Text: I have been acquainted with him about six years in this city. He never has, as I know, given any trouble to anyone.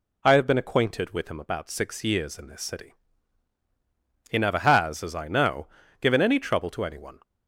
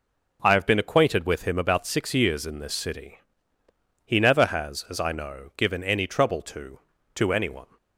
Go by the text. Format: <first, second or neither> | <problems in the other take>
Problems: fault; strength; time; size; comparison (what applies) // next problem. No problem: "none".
first | says "to" twice; at 7.1 s